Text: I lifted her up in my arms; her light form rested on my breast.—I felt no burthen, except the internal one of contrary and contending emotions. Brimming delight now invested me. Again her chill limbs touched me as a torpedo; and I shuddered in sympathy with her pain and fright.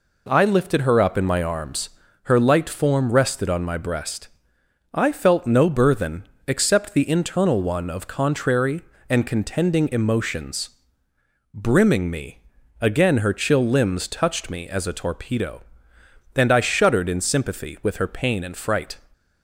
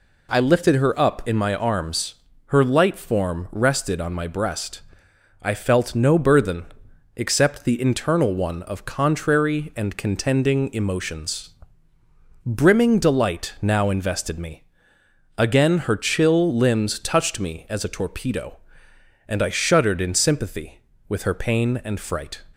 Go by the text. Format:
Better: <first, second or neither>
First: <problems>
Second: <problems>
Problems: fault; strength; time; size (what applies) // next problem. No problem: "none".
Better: second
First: skips "delight now invested"; at 12.1 s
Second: none